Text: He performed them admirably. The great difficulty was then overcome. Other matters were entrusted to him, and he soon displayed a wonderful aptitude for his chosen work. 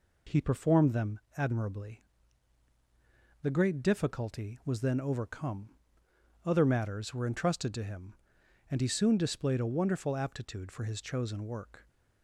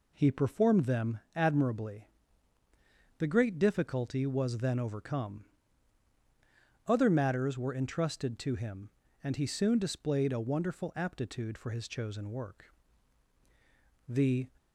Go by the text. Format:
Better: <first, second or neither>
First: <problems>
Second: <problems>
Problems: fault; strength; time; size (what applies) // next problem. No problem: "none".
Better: first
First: pauses between "them" and "admirably"; slight; at 1.1 s; 0.18 s long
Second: pauses between "them" and "admirably"; slight; at 1.1 s; 0.16 s long // goes on to say "The"; slight; from 14.0 s on; 0.40 s long